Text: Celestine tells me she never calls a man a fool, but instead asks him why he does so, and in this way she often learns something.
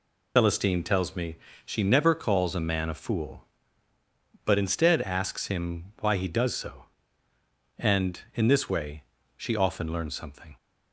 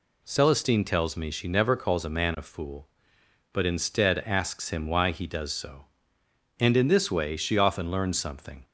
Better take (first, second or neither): second